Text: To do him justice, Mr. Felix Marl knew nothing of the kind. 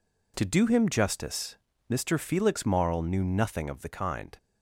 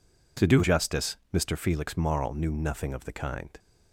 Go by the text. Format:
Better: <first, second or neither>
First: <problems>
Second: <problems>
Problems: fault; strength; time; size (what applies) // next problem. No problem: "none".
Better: first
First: none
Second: skips "him"; at 0.6 s